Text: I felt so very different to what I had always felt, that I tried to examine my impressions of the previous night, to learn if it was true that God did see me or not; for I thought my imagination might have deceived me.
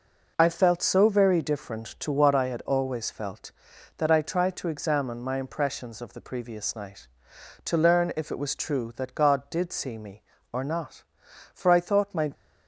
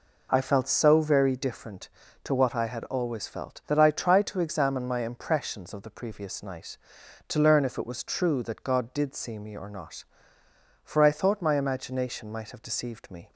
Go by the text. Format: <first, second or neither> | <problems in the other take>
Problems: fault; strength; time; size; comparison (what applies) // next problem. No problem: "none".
second | stops before "imagination might have deceived me"; at 12.3 s